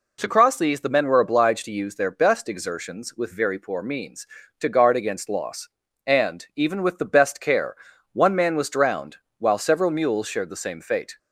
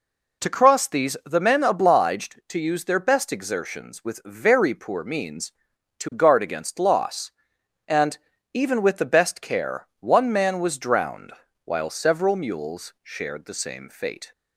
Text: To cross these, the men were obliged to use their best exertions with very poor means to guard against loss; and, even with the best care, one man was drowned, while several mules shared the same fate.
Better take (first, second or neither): first